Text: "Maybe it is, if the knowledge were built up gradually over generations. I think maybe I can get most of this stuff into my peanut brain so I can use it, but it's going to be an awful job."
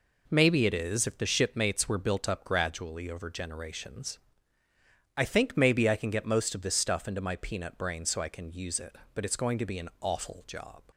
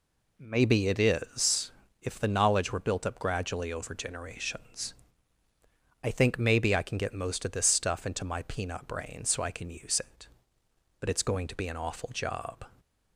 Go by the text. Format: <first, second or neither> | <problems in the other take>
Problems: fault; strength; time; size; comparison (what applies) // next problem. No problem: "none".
second | says "shipmates" for "knowledge"; at 1.2 s